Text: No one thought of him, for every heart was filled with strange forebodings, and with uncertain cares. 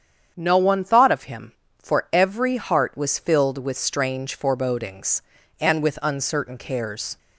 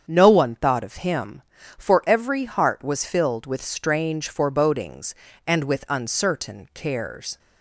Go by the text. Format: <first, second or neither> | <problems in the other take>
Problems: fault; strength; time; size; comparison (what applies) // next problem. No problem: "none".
neither | starts louder than the rest; strong; the same in both